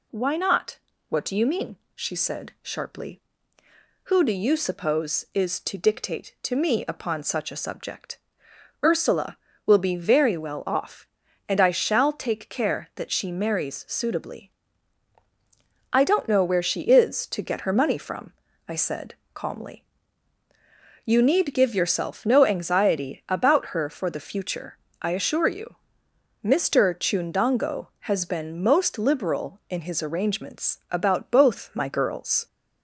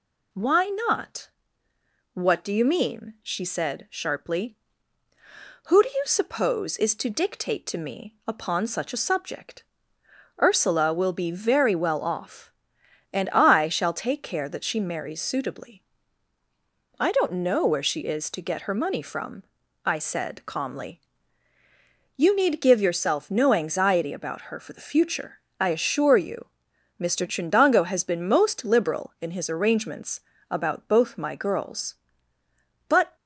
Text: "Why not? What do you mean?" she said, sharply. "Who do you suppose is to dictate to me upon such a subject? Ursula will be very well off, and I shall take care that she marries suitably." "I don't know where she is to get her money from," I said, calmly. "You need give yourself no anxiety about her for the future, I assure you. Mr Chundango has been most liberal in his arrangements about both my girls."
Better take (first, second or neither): first